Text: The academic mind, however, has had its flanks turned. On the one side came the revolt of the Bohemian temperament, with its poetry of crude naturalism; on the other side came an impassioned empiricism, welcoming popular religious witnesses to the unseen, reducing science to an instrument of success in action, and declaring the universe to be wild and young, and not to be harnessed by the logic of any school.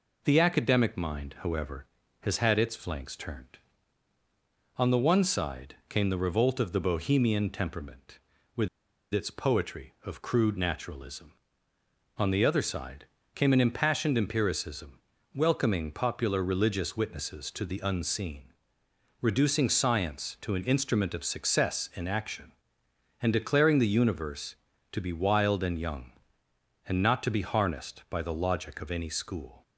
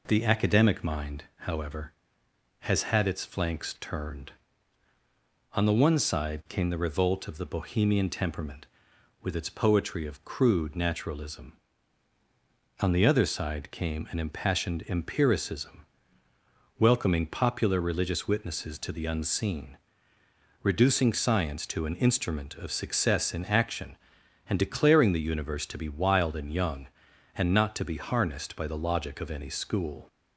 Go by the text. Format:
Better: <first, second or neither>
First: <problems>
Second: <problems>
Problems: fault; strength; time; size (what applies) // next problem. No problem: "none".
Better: second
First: pauses between "with" and "its"; at 8.6 s; 0.45 s long // pauses between "side" and "came"; slight; at 13.0 s; 0.30 s long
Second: none